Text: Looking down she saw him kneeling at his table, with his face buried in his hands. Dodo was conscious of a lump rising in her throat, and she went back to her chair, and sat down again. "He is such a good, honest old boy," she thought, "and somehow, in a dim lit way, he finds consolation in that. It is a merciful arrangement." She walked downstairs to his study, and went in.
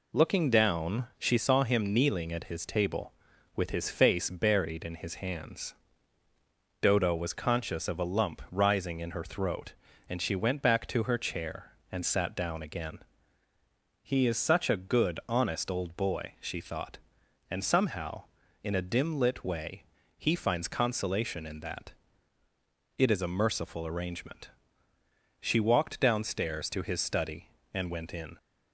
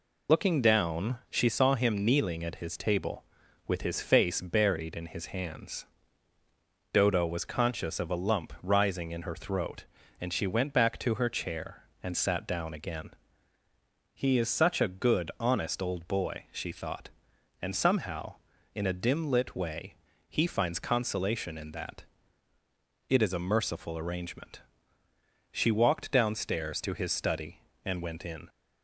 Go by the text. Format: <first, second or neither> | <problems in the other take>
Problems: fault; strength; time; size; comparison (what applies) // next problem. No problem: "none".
first | loses the start of "Looking"; at 0.2 s; 50 ms